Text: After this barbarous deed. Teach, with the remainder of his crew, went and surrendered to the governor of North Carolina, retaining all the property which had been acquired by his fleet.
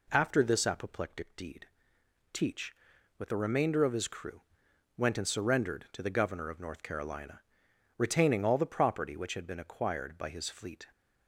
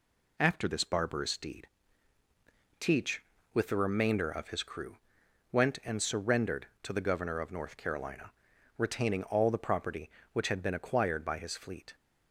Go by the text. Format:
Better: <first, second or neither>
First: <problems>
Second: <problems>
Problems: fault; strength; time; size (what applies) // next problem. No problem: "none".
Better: second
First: says "apoplectic" for "barbarous"; at 0.6 s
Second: none